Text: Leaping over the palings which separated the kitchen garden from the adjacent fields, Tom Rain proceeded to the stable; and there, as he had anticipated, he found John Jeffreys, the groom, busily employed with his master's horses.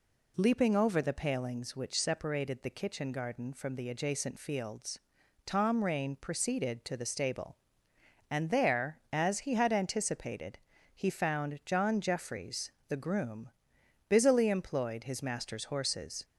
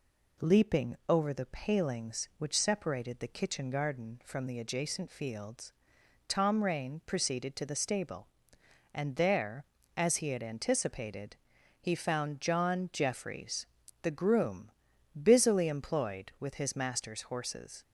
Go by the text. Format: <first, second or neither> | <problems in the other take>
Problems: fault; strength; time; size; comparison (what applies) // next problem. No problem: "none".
second | skips "with"; at 15.0 s